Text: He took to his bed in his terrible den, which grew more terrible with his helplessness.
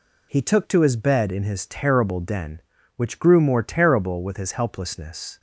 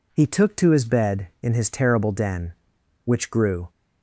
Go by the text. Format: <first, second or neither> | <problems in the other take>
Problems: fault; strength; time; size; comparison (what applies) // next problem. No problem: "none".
first | stops before "more terrible with his helplessness"; at 3.6 s